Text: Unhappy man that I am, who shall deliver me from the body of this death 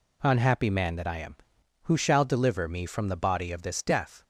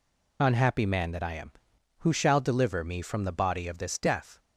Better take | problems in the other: first | loses the start of "Unhappy"; at 0.3 s; 35 ms

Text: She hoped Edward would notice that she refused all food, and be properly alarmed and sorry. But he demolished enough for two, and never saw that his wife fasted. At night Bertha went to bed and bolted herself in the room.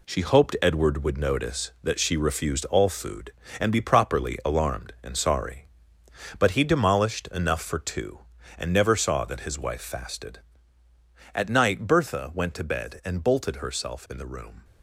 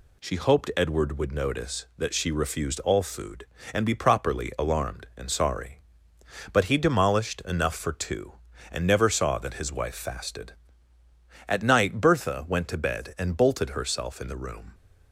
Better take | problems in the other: second | gets quieter; strong; throughout; 7.5 dB

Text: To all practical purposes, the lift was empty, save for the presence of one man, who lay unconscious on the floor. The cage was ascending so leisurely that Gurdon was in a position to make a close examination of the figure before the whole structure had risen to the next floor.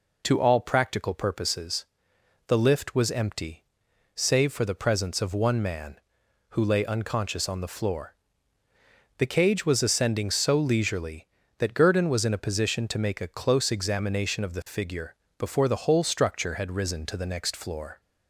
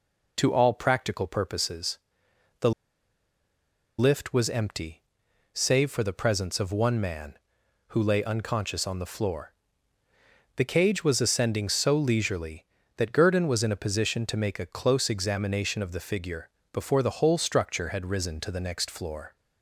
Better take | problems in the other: first | pauses between "the" and "lift"; strong; at 2.7 s; 1.2 s long // pauses between "figure" and "before"; slight; at 16.4 s; 0.24 s long; slight in the first

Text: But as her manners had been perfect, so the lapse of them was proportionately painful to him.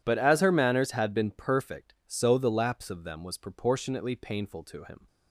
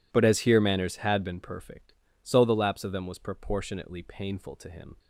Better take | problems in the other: first | says "here" for "her"; at 0.4 s

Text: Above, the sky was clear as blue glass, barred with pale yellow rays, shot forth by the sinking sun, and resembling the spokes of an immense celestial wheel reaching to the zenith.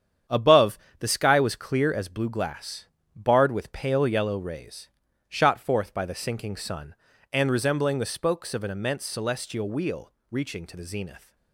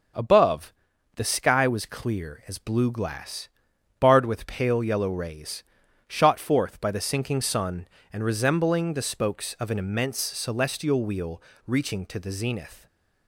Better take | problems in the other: second | gets quieter; strong; throughout; 7.5 dB // starts louder than the rest; strong; until 1.4 s; 8.5 dB; noticeable in the second // pauses between "wheel" and "reaching"; slight; at 10.1 s; 0.20 s long; slight in the second

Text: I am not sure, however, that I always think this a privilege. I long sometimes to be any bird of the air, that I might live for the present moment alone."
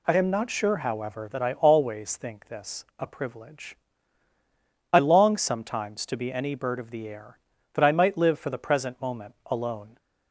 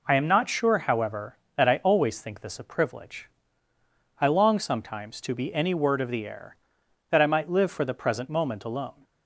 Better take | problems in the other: first | says "word" for "bird"; at 5.7 s

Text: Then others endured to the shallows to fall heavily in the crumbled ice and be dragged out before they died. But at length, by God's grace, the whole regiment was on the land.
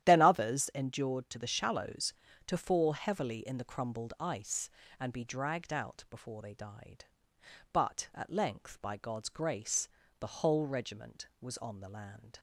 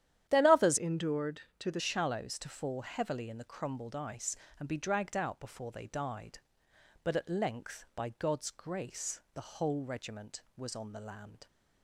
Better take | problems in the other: first | starts louder than the rest; strong; until 1.3 s; 11 dB; strong in the first // changes voice from "endured" to "the"; from 0.7 to 1.7 s; 1.0 s long

